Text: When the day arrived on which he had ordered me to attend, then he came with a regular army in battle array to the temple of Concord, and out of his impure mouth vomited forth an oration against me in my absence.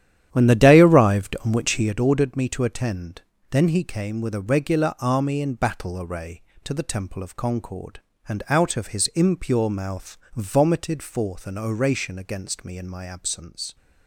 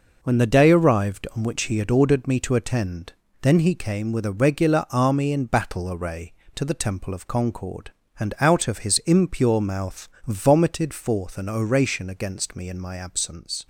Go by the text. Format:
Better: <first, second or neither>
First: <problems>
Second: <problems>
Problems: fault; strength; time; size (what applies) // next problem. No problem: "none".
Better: second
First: starts louder than the rest; strong; until 1.9 s; 10.5 dB // pauses between "mouth" and "vomited"; slight; at 10.1 s; 0.18 s long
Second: pauses between "mouth" and "vomited"; slight; at 10.0 s; 0.18 s long